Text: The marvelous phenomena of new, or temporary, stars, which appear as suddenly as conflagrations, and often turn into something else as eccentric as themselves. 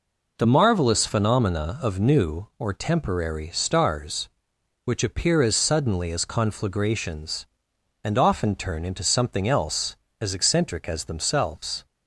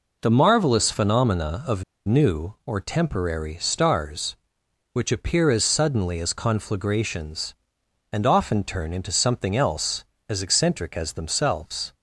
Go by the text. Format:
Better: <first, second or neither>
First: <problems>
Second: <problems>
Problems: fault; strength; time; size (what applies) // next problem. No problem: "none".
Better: first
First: none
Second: pauses between "of" and "new"; slight; at 1.8 s; 0.23 s long